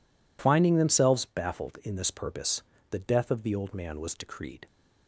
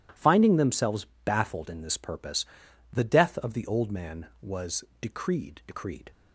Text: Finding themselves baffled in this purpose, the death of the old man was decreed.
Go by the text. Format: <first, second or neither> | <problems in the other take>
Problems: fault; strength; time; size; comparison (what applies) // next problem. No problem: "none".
first | pauses between "themselves" and "baffled"; slight; at 1.0 s; 0.18 s long // pauses between "was" and "decreed"; slight; at 4.8 s; 0.16 s long // says "decreed" twice; at 5.6 s